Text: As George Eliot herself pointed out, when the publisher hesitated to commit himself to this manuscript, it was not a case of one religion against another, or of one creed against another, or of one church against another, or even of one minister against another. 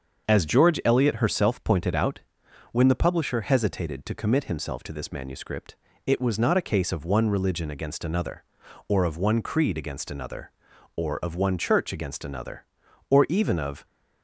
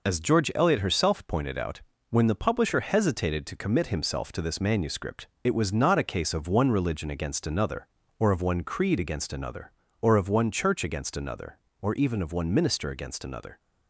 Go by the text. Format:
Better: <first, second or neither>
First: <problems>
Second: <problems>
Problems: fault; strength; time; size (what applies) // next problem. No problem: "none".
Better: second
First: starts louder than the rest; until 1.3 s; 6.5 dB // stops before "one minister against another"; at 13.8 s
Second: none